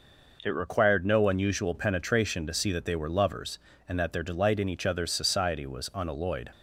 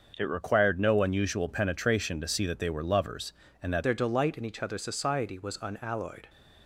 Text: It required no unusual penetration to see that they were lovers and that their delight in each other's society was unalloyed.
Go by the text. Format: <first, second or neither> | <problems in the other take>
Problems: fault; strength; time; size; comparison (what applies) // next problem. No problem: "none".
first | starts louder than the rest; until 1.1 s; 6 dB // changes voice at "their"; from 3.8 s on; 2.4 s long